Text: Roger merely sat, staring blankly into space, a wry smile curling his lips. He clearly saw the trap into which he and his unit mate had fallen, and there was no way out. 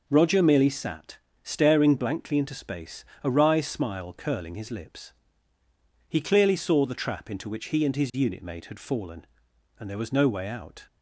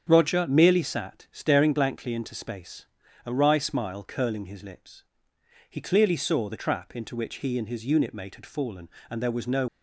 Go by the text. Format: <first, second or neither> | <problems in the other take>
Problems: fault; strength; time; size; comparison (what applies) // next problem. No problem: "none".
first | starts louder than the rest; strong; until 1.0 s; 8 dB // stops before "way out"; at 9.6 s